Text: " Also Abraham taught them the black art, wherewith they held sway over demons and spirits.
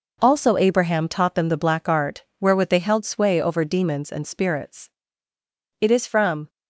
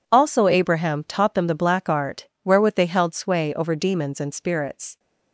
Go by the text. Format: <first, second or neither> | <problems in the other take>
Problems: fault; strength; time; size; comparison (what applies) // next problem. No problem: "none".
second | goes on to say "It is from"; noticeable; from 5.7 s on; 0.70 s long